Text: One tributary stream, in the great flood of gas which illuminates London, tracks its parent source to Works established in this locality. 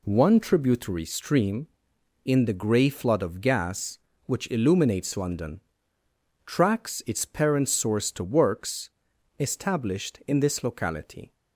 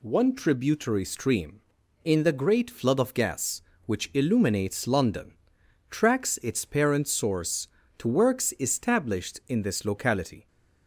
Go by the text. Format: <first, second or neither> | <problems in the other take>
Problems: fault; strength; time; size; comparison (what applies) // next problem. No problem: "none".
second | says "grey" for "great"; at 2.5 s // pauses between "Works" and "established"; noticeable; at 8.8 s; 0.50 s long